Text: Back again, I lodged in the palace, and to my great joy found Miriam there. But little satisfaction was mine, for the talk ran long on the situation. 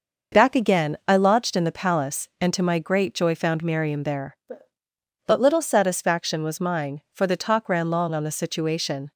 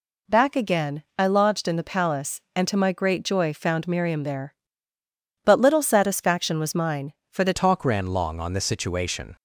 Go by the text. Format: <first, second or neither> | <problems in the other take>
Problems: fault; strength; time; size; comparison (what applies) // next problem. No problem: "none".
first | changes voice at "talk"; from 7.5 s on; 1.8 s long